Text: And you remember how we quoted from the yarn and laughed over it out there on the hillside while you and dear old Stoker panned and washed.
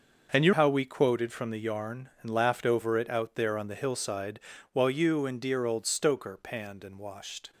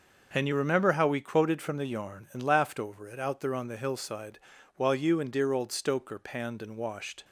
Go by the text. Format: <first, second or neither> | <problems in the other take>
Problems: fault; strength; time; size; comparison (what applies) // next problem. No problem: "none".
second | starts louder than the rest; until 1.3 s; 6 dB; noticeable in the second // skips "remember"; at 0.5 s // pauses between "hillside" and "while"; slight; at 4.3 s; 0.36 s long; also in the second